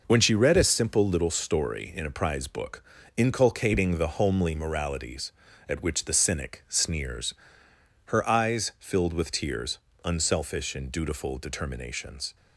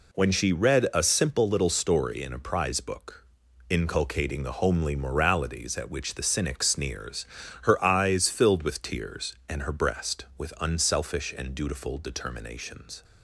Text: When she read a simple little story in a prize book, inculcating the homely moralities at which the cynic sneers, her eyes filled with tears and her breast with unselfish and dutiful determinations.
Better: second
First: skips "and her breast with"; at 9.9 s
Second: none

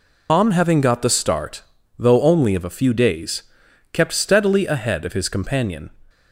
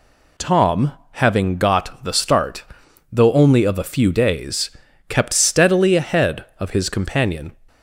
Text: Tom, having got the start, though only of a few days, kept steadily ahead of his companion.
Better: second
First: loses the start of "Tom"; at 0.2 s; 140 ms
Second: none

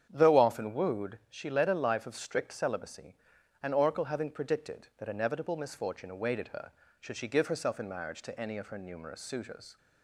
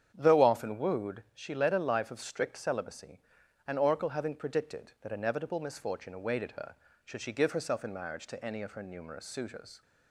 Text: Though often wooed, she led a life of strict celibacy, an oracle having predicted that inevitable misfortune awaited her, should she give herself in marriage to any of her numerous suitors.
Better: neither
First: starts louder than the rest; strong; until 1.1 s; 8.5 dB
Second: starts louder than the rest; strong; until 1.1 s; 8.5 dB

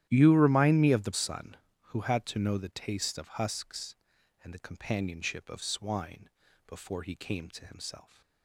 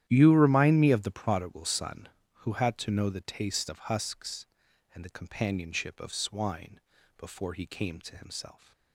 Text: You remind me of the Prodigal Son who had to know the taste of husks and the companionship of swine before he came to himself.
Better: second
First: starts louder than the rest; strong; until 1.1 s; 12 dB // skips "Prodigal"; at 1.1 s // pauses between "swine" and "before"; at 6.2 s; 0.38 s long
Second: starts louder than the rest; strong; until 1.0 s; 11.5 dB // pauses between "swine" and "before"; at 6.7 s; 0.38 s long

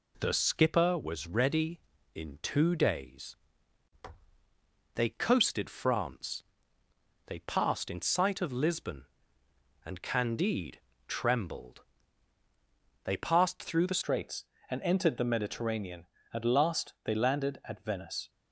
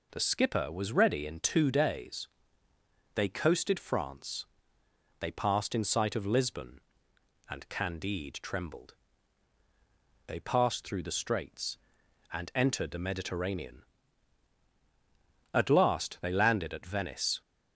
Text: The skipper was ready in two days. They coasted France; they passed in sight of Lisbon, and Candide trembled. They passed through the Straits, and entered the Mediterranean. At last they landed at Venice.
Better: second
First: pauses between "Candide" and "trembled"; slight; at 10.7 s; 0.26 s long // changes voice at "Straits"; from 14.0 s on; 4.2 s long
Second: none

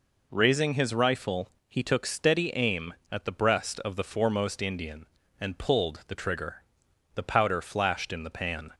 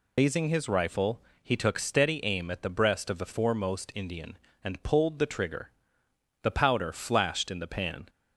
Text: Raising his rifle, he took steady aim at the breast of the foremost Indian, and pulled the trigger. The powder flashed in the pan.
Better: first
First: none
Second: loses the start of "Raising"; at 0.1 s; 115 ms

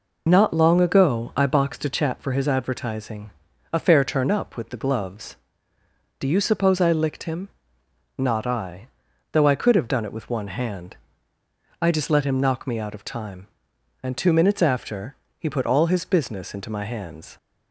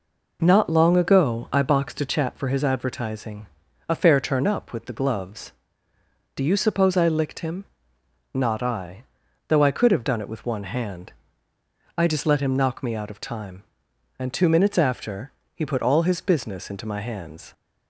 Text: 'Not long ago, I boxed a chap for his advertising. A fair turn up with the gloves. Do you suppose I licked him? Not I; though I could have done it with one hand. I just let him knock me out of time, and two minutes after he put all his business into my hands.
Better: second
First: loses the start of "Not"; at 0.2 s; 25 ms // pauses between "after" and "he"; slight; at 15.1 s; 0.22 s long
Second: pauses between "after" and "he"; slight; at 15.3 s; 0.22 s long

